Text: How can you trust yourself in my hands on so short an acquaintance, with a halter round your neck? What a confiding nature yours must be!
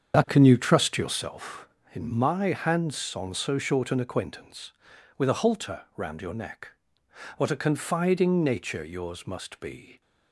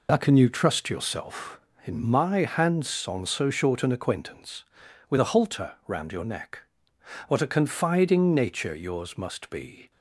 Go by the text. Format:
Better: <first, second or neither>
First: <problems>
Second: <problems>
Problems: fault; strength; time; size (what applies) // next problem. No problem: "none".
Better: second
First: starts louder than the rest; strong; until 1.2 s; 7.5 dB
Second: none